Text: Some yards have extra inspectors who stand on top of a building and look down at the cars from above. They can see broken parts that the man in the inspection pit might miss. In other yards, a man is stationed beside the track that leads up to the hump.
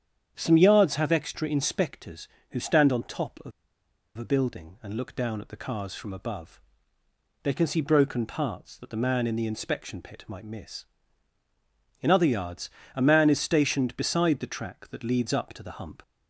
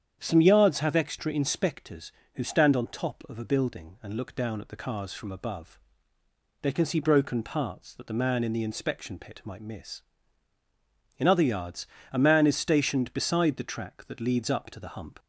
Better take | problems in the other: second | starts louder than the rest; strong; until 1.3 s; 8.5 dB; strong in the second // pauses between "of" and "a"; noticeable; at 3.5 s; 0.66 s long

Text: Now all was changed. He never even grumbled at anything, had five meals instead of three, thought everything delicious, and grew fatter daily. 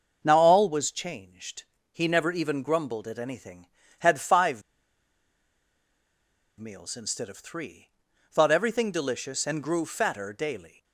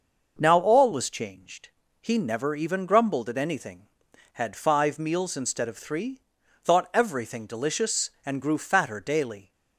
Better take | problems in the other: second | starts louder than the rest; until 1.2 s; 6 dB // pauses between "five" and "meals"; strong; at 4.6 s; 1.9 s long

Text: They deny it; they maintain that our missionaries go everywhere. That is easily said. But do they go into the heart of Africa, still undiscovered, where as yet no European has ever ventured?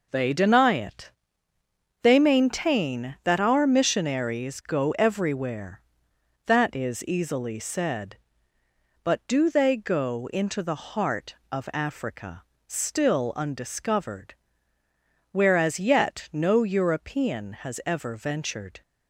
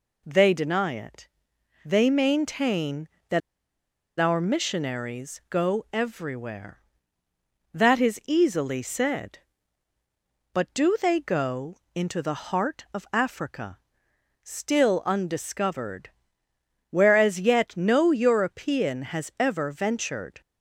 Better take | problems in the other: first | pauses between "that" and "our"; noticeable; at 3.4 s; 0.78 s long // pauses between "go" and "into"; slight; at 11.7 s; 0.18 s long

